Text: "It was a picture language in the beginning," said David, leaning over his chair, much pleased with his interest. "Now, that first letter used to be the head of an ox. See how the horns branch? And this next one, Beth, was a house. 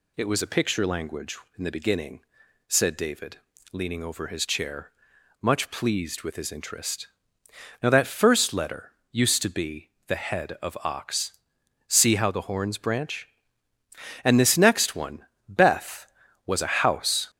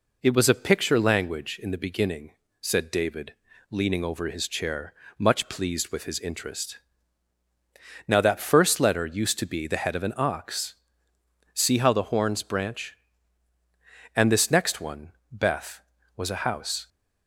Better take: second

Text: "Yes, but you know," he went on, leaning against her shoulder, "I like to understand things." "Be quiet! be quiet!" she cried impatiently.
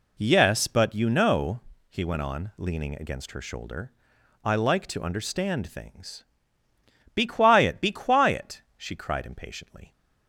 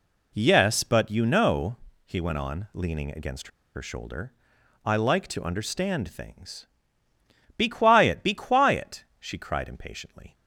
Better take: first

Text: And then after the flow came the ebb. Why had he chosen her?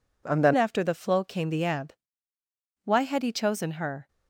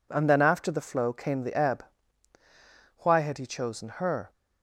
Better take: second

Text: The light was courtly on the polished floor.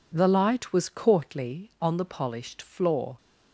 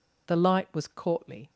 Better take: first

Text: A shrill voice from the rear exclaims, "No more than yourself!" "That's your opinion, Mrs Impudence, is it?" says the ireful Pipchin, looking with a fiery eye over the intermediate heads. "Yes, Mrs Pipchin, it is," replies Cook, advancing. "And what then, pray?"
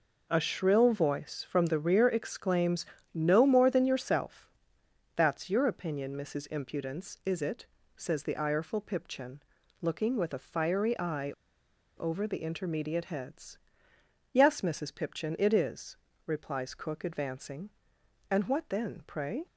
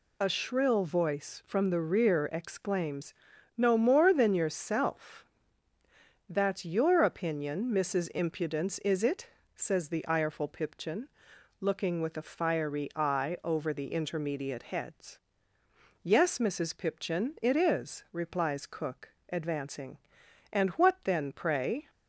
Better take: second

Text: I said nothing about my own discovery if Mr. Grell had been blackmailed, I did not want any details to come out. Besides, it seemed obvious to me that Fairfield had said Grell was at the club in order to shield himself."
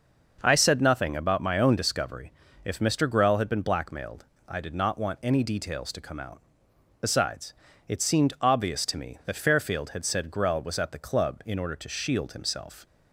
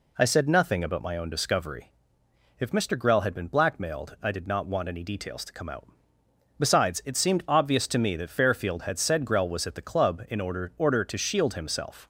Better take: first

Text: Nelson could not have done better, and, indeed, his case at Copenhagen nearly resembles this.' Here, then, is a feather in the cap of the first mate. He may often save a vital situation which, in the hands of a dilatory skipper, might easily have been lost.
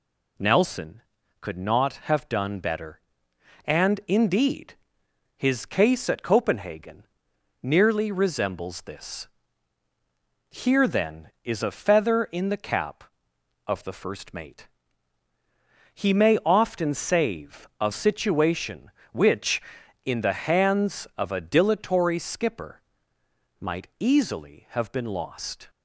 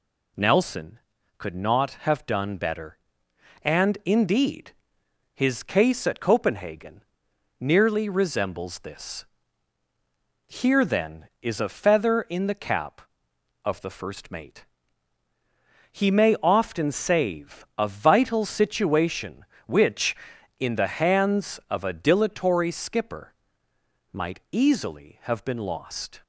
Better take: second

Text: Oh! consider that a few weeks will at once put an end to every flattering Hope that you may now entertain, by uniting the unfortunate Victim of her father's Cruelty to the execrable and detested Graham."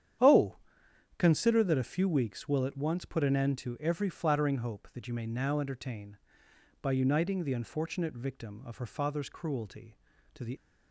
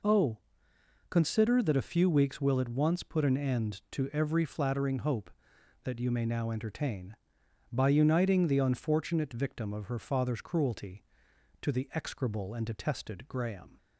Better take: second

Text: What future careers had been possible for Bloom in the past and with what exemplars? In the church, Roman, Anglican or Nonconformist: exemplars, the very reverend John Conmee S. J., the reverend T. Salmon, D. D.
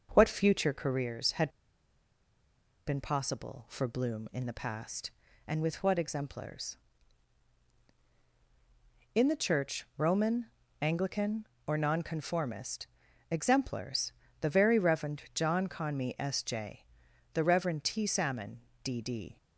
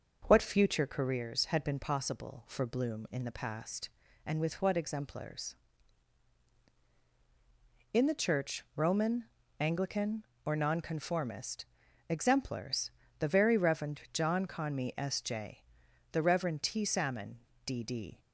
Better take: second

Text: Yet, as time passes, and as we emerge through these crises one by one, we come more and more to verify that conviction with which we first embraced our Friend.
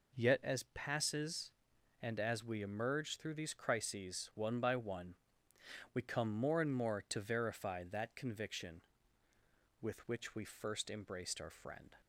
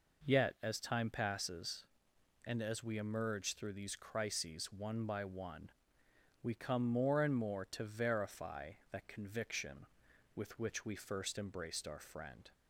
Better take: second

